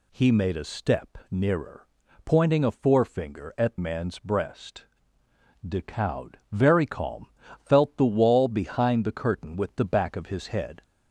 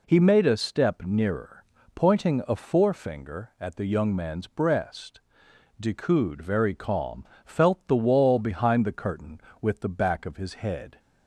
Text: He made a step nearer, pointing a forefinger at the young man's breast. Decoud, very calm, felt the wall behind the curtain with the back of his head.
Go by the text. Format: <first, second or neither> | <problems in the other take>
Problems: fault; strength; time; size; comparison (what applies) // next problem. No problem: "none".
second | skips "the young"; at 3.7 s